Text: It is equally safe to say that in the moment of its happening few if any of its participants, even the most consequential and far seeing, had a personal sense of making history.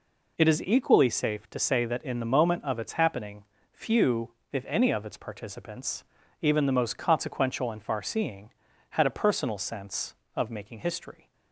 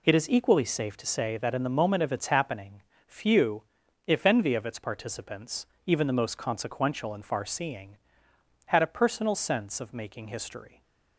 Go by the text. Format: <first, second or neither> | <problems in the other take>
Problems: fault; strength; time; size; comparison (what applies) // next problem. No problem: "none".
first | pauses between "happening" and "few"; slight; at 2.8 s; 0.26 s long; slight in the first // pauses between "few" and "if"; at 3.6 s; 0.42 s long; slight in the first // says "envy" for "any"; at 4.2 s // stays silent after the last word; slight; from 10.6 s on; 0.5 s long